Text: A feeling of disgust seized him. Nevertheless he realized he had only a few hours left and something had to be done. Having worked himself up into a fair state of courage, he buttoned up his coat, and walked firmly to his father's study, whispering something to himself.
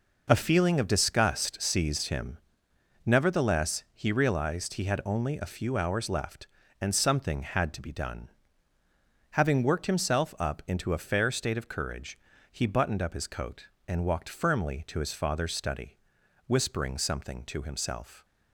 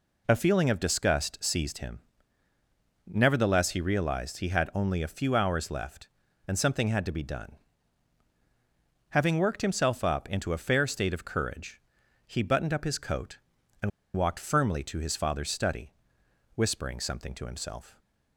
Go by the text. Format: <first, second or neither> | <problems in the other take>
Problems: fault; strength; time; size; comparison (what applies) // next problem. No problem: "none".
first | pauses between "and" and "walked"; slight; at 13.9 s; 0.26 s long